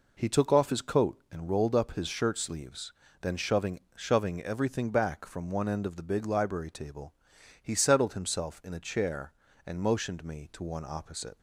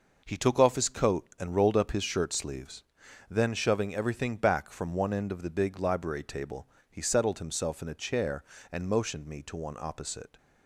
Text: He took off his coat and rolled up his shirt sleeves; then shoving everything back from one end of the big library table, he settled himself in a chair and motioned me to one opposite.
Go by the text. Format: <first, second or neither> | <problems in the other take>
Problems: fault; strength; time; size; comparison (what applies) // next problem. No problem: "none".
second | says "shoving" twice; at 3.9 s